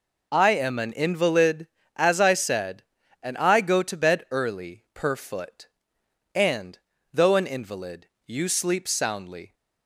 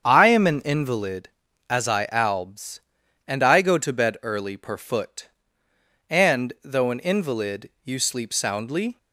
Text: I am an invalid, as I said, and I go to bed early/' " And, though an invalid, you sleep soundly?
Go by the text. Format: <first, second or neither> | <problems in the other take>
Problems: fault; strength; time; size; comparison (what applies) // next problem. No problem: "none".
first | starts louder than the rest; strong; until 1.1 s; 8 dB // says "albs" for "said"; at 2.1 s